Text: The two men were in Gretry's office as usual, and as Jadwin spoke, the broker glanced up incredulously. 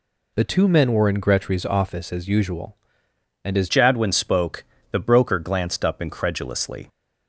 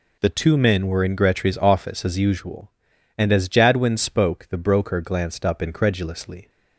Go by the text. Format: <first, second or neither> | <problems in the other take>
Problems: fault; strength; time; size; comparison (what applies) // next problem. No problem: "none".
second | changes voice at "Jadwin"; from 3.6 s on; 3.2 s long